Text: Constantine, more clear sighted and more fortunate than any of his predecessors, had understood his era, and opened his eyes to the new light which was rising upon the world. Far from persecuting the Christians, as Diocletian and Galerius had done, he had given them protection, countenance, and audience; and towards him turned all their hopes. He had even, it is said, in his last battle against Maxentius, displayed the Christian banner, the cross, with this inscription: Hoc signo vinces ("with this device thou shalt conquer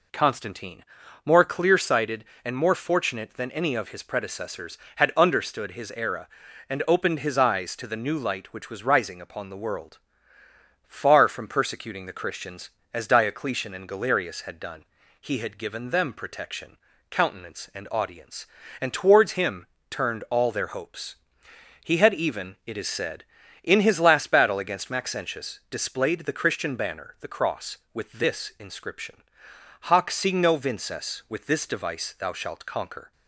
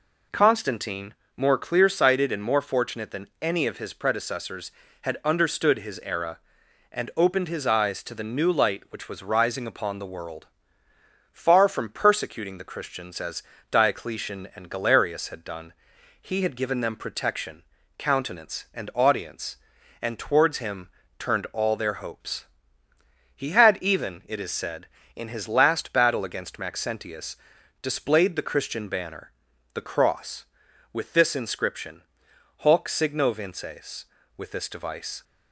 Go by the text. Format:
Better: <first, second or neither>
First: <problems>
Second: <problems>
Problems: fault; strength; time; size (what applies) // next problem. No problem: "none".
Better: first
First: pauses between "him" and "turned"; slight; at 19.6 s; 0.22 s long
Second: pauses between "as" and "Diocletian"; slight; at 13.4 s; 0.28 s long // pauses between "him" and "turned"; slight; at 20.8 s; 0.28 s long // stops before "thou shalt conquer"; at 35.2 s